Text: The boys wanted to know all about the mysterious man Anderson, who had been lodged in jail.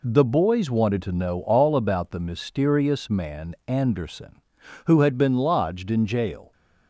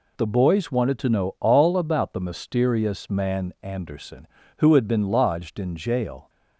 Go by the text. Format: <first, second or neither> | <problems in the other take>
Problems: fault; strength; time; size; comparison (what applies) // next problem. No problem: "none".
neither | none